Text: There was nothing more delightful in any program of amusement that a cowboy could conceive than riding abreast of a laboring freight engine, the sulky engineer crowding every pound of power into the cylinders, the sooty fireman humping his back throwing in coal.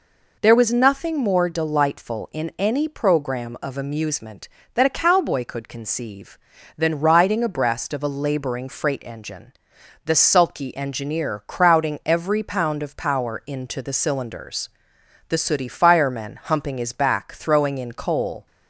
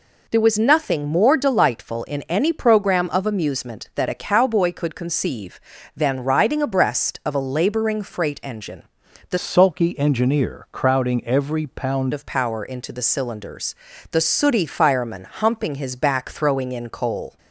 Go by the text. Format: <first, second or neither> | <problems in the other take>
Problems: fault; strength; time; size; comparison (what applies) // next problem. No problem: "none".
first | changes voice from "sulky" to "pound"; from 9.3 to 12.1 s; 2.8 s long